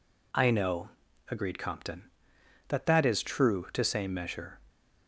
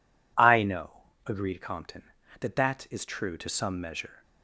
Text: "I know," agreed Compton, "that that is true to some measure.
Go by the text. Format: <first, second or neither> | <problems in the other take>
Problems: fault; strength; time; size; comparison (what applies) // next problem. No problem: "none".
second | says "same" for "some"; at 3.8 s